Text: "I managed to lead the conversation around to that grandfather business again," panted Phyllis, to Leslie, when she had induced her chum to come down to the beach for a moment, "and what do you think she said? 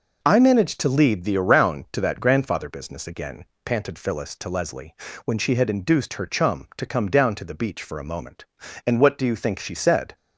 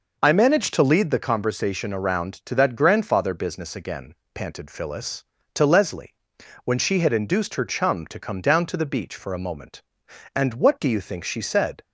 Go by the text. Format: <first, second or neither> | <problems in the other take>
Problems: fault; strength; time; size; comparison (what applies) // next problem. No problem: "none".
second | skips "conversation"; at 1.3 s